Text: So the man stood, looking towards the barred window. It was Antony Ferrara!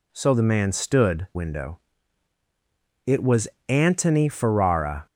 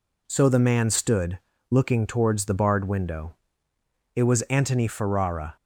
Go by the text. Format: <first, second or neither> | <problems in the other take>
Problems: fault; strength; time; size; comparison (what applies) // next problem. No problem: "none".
second | skips "looking towards the barred"; at 1.3 s // pauses between "was" and "Antony"; slight; at 3.4 s; 0.20 s long